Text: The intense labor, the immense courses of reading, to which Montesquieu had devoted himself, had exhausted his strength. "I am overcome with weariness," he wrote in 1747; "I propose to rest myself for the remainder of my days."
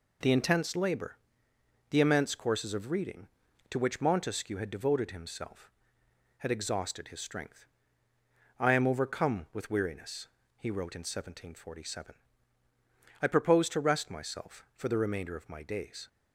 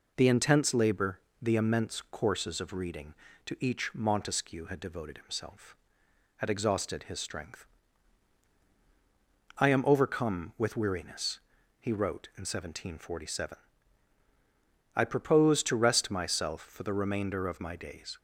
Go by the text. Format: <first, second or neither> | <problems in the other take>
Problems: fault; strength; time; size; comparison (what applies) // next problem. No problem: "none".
first | says "each" for "which"; at 3.5 s